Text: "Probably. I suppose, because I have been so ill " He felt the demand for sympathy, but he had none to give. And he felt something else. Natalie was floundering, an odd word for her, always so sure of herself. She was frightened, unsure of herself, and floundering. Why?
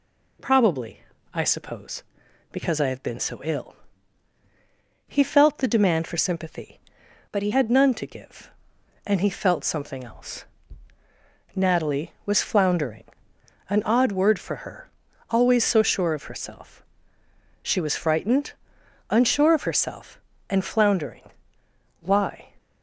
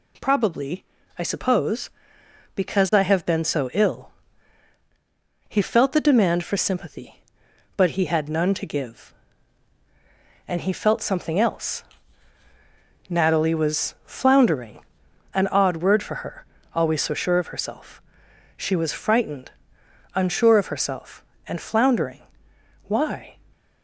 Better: second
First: changes voice from "but" to "he"; from 7.3 to 7.5 s; 0.2 s long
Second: none

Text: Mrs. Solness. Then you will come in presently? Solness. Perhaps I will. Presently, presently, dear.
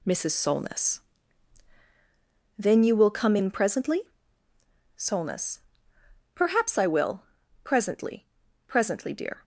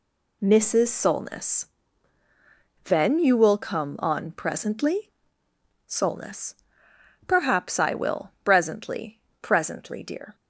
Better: first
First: none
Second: says "on" for "in"; at 3.9 s

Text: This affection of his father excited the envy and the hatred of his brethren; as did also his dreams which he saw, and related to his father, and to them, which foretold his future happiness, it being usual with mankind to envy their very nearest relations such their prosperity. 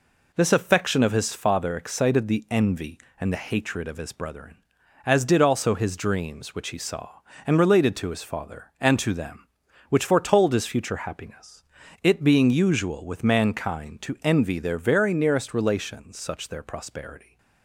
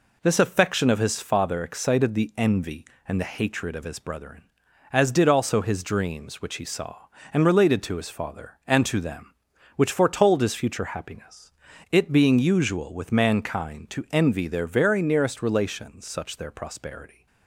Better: neither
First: none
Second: none

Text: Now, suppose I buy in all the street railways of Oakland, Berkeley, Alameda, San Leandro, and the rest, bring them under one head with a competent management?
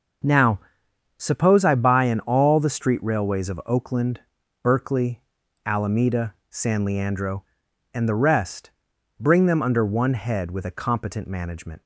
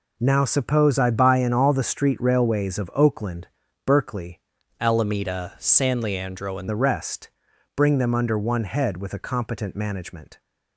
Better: first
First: none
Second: changes voice from "Alameda" to "and"; from 4.8 to 6.6 s; 1.8 s long

